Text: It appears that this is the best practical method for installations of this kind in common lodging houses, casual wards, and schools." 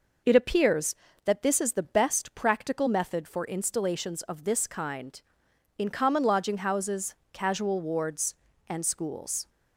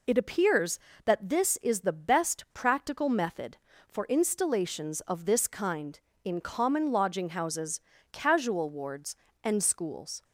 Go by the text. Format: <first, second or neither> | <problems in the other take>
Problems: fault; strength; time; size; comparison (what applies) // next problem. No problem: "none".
neither | none